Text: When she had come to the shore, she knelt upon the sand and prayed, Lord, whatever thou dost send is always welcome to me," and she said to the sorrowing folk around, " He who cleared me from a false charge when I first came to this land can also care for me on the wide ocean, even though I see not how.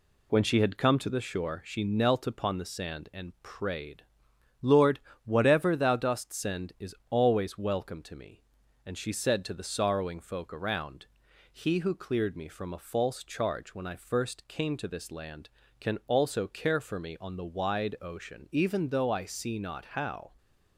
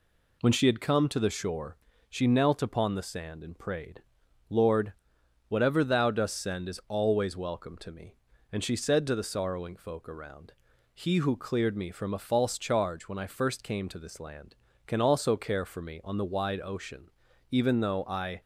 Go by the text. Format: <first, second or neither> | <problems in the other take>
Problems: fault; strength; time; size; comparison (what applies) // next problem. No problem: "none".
first | stops before "see not how"; at 18.4 s